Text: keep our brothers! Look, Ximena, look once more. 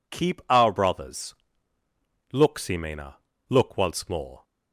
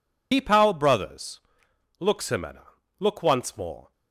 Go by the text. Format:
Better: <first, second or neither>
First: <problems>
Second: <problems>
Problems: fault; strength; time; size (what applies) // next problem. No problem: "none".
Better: first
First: none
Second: loses the start of "keep"; at 0.3 s; 80 ms